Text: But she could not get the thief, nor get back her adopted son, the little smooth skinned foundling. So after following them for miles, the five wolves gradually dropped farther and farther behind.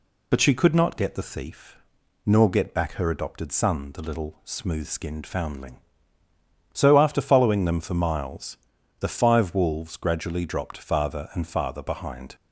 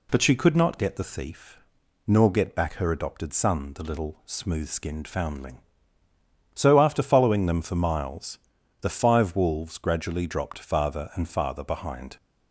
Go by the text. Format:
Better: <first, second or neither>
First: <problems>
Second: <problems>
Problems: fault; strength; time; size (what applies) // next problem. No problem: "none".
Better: second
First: loses the start of "But"; at 0.3 s; 40 ms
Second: none